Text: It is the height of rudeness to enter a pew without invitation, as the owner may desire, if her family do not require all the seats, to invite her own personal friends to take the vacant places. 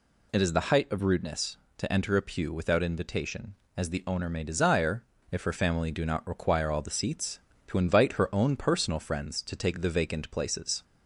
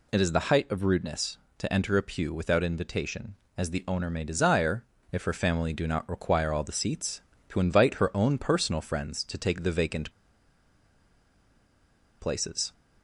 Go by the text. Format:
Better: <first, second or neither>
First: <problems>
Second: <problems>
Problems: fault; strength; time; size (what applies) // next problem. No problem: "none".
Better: first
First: none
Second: pauses between "vacant" and "places"; strong; at 10.1 s; 2.0 s long